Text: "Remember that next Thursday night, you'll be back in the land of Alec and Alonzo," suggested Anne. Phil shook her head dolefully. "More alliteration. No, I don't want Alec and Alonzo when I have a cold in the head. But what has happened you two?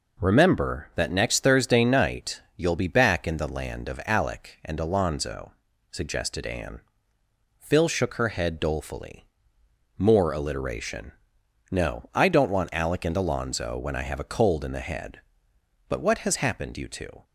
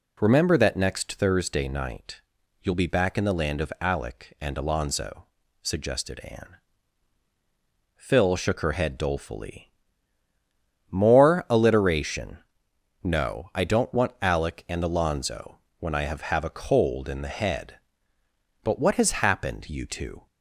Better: first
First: none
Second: pauses between "Alonzo" and "when"; slight; at 15.5 s; 0.20 s long // says "have" twice; at 16.2 s

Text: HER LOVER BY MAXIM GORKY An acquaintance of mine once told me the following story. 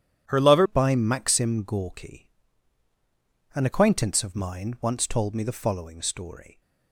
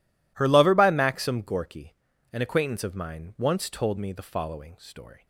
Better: second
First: starts louder than the rest; strong; until 1.2 s; 10 dB // changes voice at "BY"; from 0.6 s on; 6.0 s long // pauses between "GORKY" and "An"; at 2.3 s; 1.2 s long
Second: pauses between "GORKY" and "An"; at 1.9 s; 0.38 s long

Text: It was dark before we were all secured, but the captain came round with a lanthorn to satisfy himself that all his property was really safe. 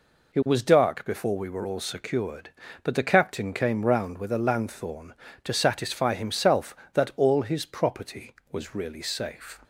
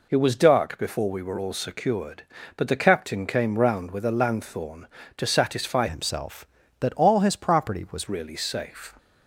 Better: first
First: none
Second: changes voice from "himself" to "was"; from 5.8 to 8.0 s; 2.2 s long

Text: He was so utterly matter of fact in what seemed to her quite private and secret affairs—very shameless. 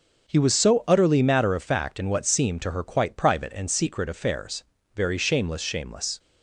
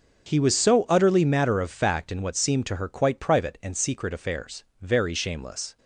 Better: second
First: starts louder than the rest; until 1.3 s; 7 dB // says "shameless" twice; at 5.6 s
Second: starts louder than the rest; until 1.3 s; 6.5 dB

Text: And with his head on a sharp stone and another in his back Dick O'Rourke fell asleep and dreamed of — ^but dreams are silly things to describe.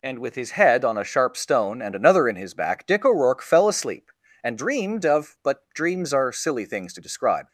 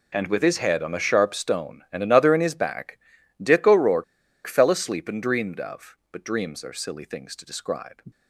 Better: first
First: none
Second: pauses between "back" and "Dick"; at 2.9 s; 0.42 s long // pauses between "O'Rourke" and "fell"; at 4.0 s; 0.43 s long

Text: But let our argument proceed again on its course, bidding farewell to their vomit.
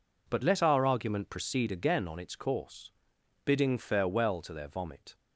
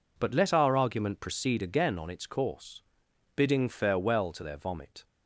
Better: neither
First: none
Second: none

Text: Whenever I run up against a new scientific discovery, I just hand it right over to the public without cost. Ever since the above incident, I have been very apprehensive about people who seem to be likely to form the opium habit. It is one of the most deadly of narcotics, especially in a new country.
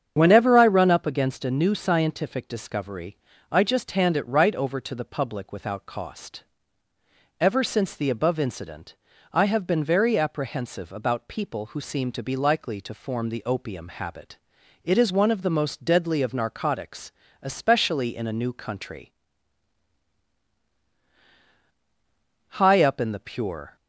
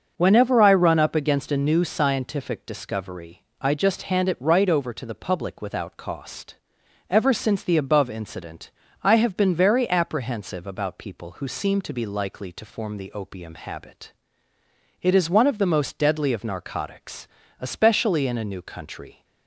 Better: second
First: starts louder than the rest; strong; until 1.1 s; 8 dB // goes on to say "High up in the pure"; noticeable; from 22.5 s on; 1.2 s long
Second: starts louder than the rest; until 1.1 s; 6.5 dB

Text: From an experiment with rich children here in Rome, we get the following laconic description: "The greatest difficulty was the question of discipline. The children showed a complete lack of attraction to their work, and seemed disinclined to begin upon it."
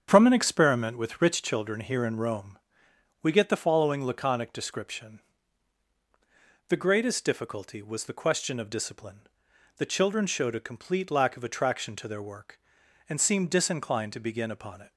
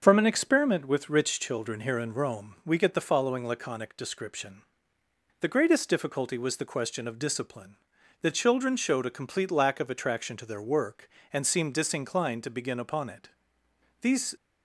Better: first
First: starts louder than the rest; strong; until 1.1 s; 7.5 dB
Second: starts louder than the rest; until 1.0 s; 7 dB // goes on to say "These"; slight; from 14.0 s on; 0.34 s long

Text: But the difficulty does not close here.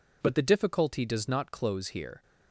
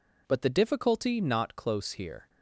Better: first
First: none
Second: skips "does"; at 1.2 s

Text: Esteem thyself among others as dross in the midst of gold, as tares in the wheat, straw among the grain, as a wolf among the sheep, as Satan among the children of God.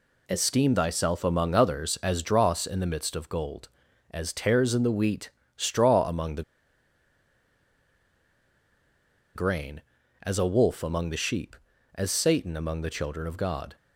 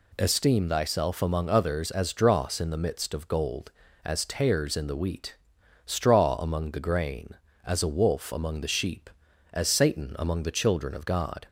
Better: second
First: pauses between "the" and "grain"; strong; at 6.4 s; 2.9 s long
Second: none

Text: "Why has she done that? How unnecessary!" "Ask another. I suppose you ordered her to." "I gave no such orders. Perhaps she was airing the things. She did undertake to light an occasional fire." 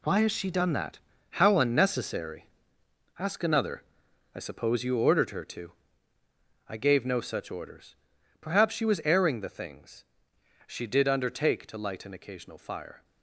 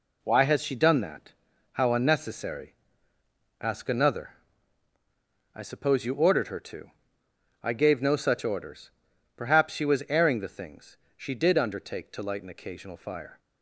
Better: second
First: gets quieter; strong; throughout; 10.5 dB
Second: none

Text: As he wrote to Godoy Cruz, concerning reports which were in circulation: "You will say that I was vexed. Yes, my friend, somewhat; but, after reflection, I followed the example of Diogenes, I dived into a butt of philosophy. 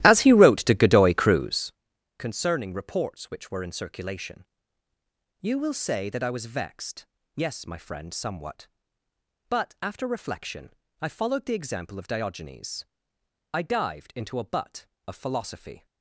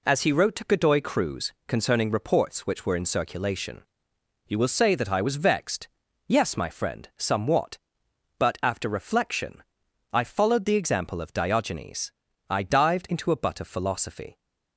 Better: second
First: starts louder than the rest; strong; until 1.7 s; 15 dB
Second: none

